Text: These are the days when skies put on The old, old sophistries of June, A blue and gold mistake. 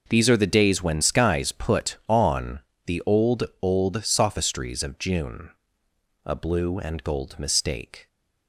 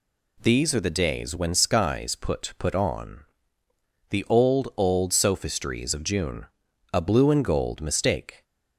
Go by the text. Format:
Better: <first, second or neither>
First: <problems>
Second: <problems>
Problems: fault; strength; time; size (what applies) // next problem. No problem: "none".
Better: first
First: pauses between "on" and "The"; slight; at 2.5 s; 0.26 s long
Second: says "put" twice; at 2.6 s // pauses between "on" and "The"; noticeable; at 3.2 s; 0.86 s long